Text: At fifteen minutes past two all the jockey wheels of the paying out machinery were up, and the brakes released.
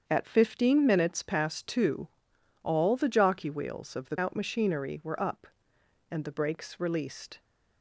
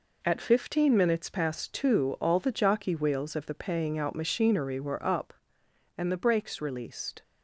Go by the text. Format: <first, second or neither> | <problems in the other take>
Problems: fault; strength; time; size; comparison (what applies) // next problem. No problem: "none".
second | starts louder than the rest; strong; until 1.0 s; 7.5 dB // pauses between "two" and "all"; noticeable; at 2.0 s; 0.54 s long // skips "paying"; at 4.1 s